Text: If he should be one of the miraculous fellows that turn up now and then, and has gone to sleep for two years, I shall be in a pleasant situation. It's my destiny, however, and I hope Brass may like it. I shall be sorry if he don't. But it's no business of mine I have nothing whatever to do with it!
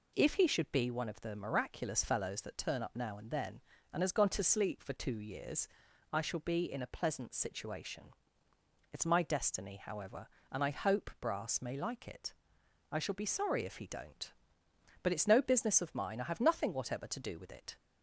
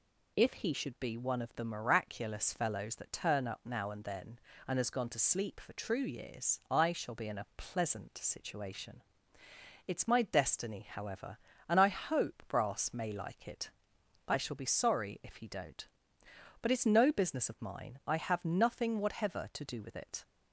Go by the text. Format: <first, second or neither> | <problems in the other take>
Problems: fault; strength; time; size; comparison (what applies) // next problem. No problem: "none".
first | says "true" for "two"; at 5.7 s